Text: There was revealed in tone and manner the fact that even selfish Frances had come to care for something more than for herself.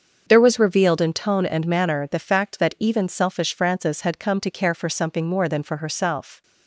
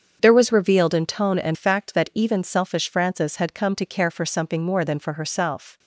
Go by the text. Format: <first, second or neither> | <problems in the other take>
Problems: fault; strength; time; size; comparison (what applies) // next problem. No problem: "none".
first | starts louder than the rest; strong; until 1.2 s; 7.5 dB; also in the first // skips "manner the"; at 1.5 s